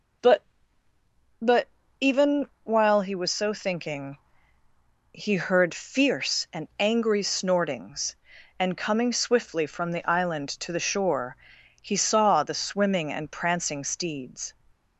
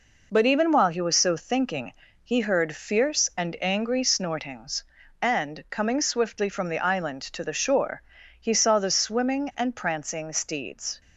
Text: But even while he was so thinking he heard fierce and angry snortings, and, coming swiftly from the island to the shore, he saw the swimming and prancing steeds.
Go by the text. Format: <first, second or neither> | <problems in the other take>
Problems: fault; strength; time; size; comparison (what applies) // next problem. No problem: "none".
second | says "But" twice; at 1.3 s // pauses between "thinking" and "he"; noticeable; at 4.1 s; 0.94 s long; slight in the second